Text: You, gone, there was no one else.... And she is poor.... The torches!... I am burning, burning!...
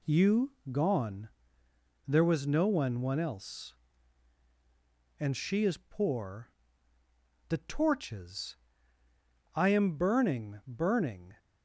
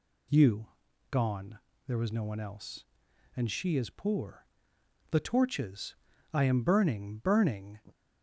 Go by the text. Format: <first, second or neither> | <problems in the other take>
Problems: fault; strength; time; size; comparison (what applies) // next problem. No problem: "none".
second | says "one" twice; at 3.0 s